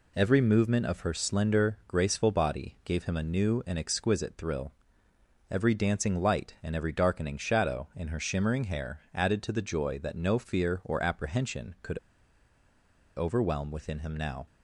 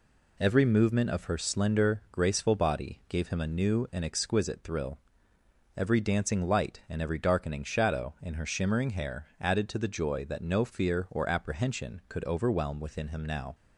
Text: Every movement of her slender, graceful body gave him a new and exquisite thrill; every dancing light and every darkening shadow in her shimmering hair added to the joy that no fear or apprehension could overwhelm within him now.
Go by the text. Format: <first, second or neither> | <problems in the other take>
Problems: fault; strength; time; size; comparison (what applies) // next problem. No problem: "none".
second | pauses between "could" and "overwhelm"; at 11.9 s; 1.1 s long